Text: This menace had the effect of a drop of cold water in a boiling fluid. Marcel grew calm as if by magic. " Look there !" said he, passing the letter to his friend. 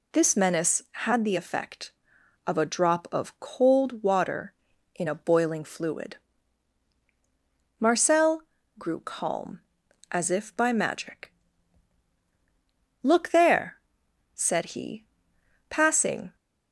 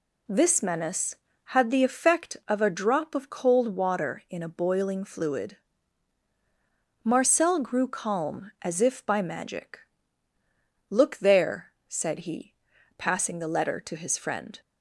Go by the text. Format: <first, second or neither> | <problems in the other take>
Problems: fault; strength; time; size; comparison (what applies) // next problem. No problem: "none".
second | pauses between "Marcel" and "grew"; slight; at 8.4 s; 0.36 s long // stops before "the letter to his friend"; at 16.3 s